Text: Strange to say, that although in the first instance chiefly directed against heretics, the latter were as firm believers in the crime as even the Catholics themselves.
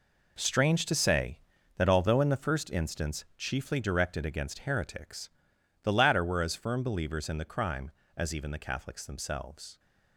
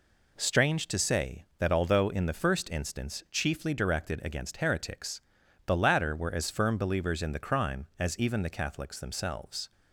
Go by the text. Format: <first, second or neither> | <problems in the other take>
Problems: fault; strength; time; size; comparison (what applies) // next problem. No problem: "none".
second | gets quieter; strong; throughout; 11.5 dB